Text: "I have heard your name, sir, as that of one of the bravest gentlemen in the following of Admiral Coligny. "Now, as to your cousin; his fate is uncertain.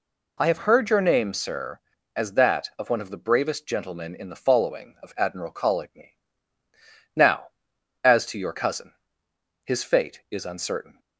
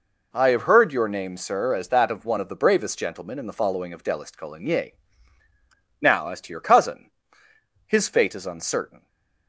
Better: first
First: none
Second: says "Delist" for "Admiral"; at 4.0 s // stays silent after the last word; slight; from 8.9 s on; 0.5 s long

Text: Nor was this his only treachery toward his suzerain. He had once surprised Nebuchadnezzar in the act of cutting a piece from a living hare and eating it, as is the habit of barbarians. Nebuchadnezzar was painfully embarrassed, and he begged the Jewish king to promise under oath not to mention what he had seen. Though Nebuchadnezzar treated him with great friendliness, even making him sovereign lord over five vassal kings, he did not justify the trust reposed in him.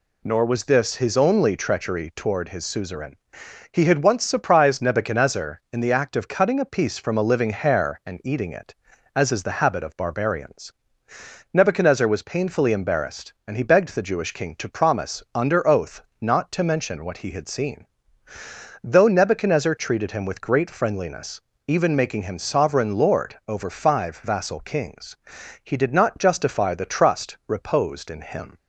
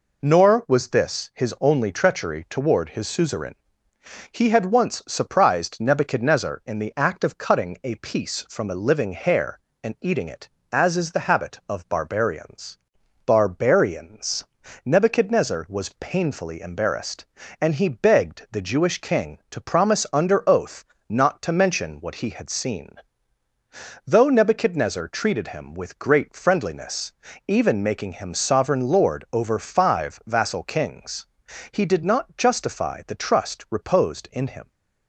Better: first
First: pauses between "oath" and "not"; slight; at 16.0 s; 0.18 s long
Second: says "barbarians" twice; at 13.2 s // pauses between "oath" and "not"; slight; at 20.8 s; 0.24 s long

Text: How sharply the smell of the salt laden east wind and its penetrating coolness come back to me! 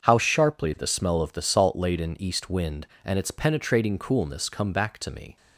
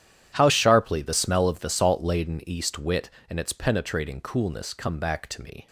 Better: first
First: starts louder than the rest; until 1.0 s; 6.5 dB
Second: starts louder than the rest; strong; until 1.3 s; 10.5 dB // says "wit" for "wind"; at 2.7 s

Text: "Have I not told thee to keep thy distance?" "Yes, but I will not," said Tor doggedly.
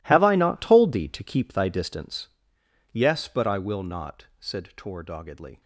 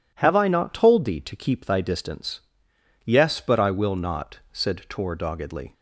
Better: second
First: gets quieter; strong; throughout; 16 dB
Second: none

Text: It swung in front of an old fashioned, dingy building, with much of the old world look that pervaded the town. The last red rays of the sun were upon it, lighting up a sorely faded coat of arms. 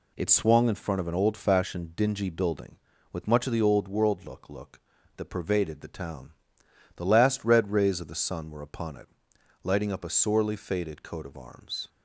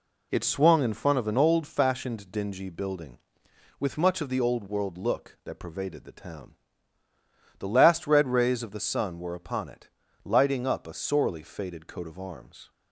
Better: second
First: says "look" twice; at 4.4 s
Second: none

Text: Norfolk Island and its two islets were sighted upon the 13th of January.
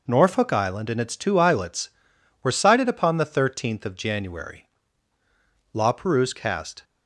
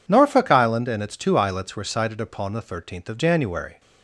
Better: second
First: goes on to say "La Perouse cast"; noticeable; from 5.7 s on; 1.1 s long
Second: none

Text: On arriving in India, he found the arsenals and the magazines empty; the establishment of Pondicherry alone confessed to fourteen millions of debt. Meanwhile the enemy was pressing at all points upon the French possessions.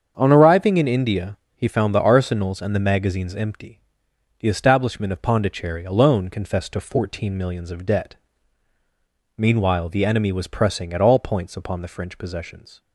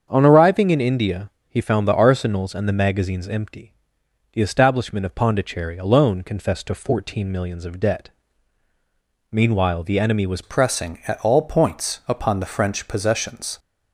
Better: first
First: starts louder than the rest; strong; until 1.1 s; 7 dB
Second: starts louder than the rest; strong; until 1.1 s; 7 dB // changes voice at "pressing"; from 10.4 s on; 3.1 s long

